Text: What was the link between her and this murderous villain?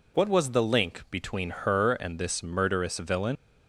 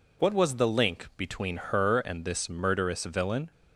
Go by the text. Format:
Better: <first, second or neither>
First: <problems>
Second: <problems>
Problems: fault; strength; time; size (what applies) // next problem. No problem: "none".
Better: second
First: leaves "villain" unfinished; at 3.3 s; 85 ms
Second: none